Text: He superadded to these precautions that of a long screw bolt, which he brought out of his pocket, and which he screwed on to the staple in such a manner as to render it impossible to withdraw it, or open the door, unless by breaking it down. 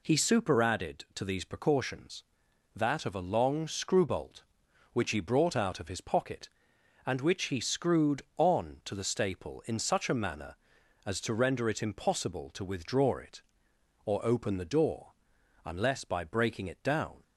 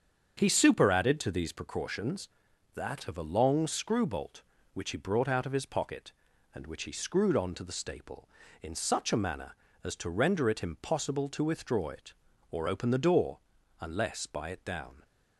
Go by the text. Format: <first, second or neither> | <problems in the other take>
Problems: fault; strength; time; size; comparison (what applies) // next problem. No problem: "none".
first | starts louder than the rest; strong; until 1.4 s; 7.5 dB // skips "breaking"; at 14.5 s